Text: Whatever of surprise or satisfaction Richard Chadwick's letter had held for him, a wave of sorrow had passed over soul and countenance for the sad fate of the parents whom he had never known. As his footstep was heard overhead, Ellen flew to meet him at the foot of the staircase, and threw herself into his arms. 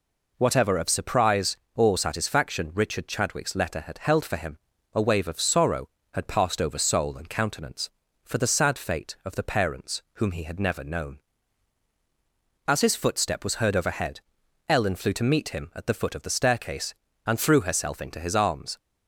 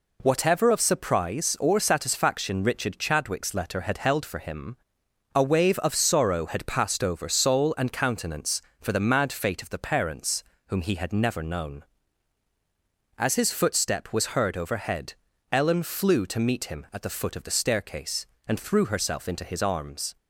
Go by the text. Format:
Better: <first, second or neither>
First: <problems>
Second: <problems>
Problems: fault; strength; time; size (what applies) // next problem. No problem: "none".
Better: first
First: none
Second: says "mad" for "sad"; at 9.0 s // pauses between "parents" and "whom"; slight; at 10.4 s; 0.22 s long